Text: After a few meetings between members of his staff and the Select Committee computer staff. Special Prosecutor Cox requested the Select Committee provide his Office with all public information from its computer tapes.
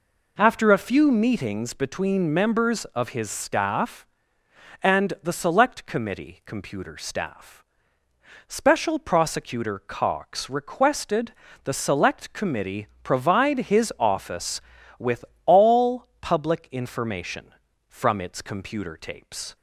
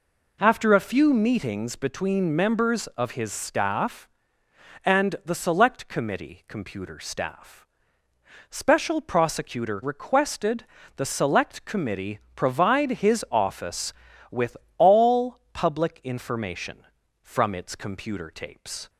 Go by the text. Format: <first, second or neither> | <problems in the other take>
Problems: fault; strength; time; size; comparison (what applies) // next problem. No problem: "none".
first | skips "Cox"; at 9.8 s // pauses between "requested" and "the"; slight; at 10.6 s; 0.30 s long; slight in the first // pauses between "Committee" and "provide"; slight; at 12.1 s; 0.18 s long; slight in the first // pauses between "with" and "all"; slight; at 14.5 s; 0.22 s long; slight in the first // pauses between "all" and "public"; slight; at 15.3 s; 0.16 s long; slight in the first